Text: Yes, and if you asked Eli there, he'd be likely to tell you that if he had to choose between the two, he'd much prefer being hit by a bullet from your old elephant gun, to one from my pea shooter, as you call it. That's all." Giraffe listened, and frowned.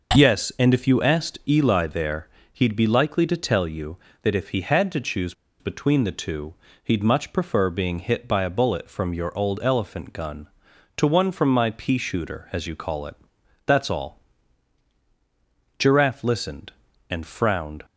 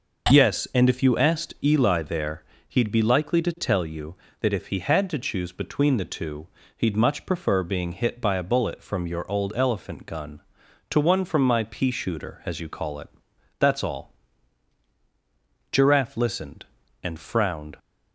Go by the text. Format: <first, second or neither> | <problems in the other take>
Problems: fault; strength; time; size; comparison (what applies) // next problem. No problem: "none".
second | pauses between "choose" and "between"; slight; at 5.3 s; 0.27 s long